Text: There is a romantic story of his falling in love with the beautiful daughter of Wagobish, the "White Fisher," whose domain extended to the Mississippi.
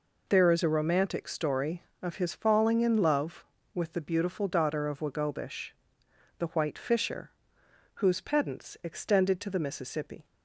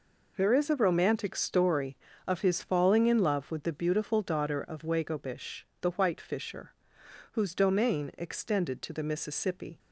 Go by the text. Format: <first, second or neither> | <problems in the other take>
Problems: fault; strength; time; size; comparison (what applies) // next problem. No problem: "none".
second | says "pedants" for "domain"; at 8.2 s